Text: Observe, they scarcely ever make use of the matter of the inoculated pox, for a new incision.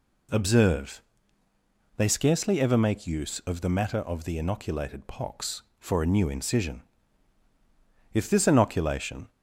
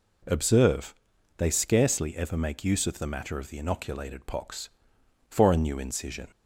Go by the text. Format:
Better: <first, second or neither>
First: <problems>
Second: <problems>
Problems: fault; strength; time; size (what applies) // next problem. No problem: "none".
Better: second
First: goes on to say "If this inoculation"; noticeable; from 8.1 s on; 1.1 s long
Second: none